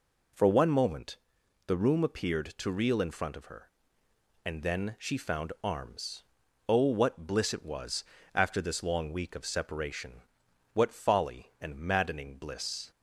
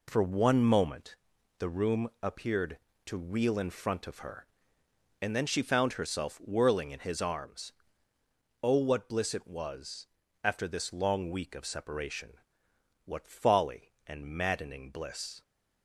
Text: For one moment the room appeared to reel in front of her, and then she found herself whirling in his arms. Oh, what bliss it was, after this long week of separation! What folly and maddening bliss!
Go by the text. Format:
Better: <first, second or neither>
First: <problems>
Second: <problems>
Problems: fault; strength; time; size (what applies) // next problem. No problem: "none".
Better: second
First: pauses between "moment" and "the"; noticeable; at 1.1 s; 0.50 s long // skips "herself whirling in his"; at 5.5 s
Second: pauses between "moment" and "the"; at 1.1 s; 0.42 s long